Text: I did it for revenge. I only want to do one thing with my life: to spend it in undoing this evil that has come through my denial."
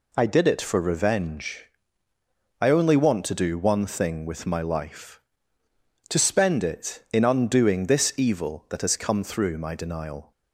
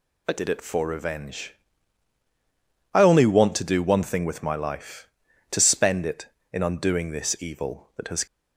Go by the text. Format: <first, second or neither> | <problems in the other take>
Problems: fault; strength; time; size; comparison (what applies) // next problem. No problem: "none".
first | stops before "come through my denial"; at 8.2 s